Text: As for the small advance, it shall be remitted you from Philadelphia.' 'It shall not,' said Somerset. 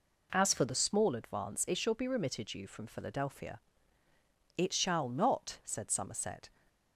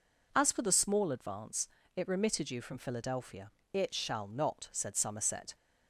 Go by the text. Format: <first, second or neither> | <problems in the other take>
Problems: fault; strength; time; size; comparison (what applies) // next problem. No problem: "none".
first | skips "shall be"; at 2.0 s